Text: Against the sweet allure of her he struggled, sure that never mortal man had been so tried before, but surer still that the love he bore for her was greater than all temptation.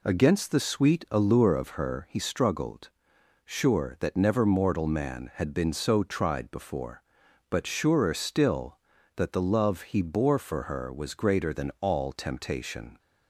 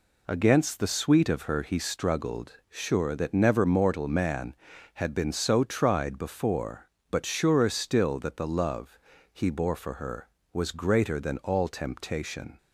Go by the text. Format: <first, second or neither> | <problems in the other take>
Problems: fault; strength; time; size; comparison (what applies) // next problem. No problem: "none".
first | skips "allure"; at 1.2 s // pauses between "love" and "he"; slight; at 8.9 s; 0.34 s long